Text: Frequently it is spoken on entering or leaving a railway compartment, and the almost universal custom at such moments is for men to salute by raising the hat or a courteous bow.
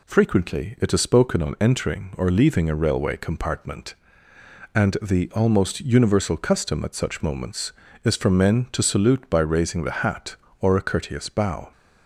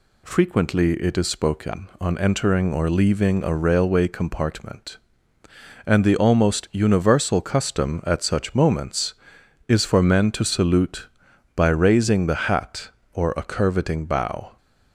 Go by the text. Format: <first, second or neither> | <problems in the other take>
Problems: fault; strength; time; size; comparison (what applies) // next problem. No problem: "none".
first | says "curveting" for "courteous"; at 13.4 s